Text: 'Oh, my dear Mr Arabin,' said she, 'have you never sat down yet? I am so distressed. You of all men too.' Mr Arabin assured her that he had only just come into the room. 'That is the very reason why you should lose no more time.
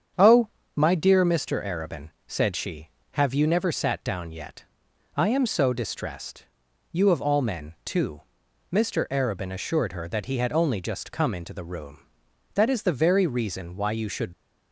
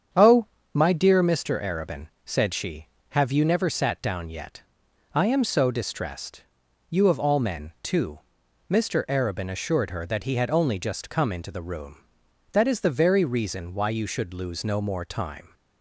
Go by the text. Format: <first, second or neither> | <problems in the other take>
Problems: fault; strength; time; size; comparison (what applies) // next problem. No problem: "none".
second | starts louder than the rest; strong; until 1.4 s; 8 dB; strong in the second // stops before "lose no more time"; at 14.3 s